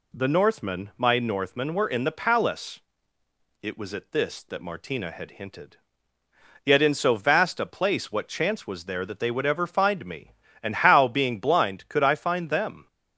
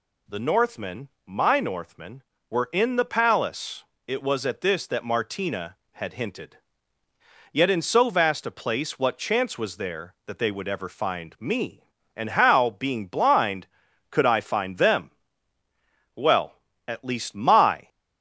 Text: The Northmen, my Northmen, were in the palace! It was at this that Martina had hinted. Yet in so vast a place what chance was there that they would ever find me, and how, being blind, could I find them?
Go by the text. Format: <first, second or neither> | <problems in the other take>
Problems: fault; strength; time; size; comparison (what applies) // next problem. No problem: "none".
first | goes on to say "Well at least my"; strong; from 16.1 s on; 1.7 s long